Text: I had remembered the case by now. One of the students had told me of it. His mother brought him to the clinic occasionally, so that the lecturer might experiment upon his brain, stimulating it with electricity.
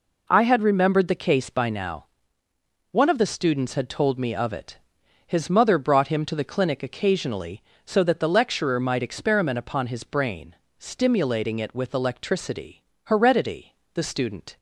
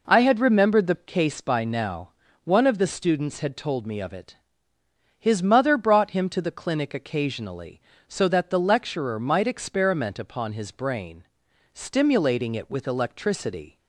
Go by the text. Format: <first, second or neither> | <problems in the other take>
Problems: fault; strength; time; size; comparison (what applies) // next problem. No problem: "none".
second | goes on to say "Heredity the student"; from 13.0 s on; 1.5 s long